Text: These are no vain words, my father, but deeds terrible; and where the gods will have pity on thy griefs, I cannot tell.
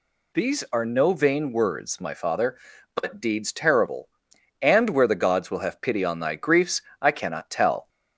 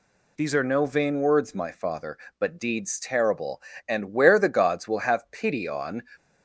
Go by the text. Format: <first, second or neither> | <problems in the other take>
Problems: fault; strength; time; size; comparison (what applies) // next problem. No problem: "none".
first | stops before "thy griefs I cannot tell"; at 6.1 s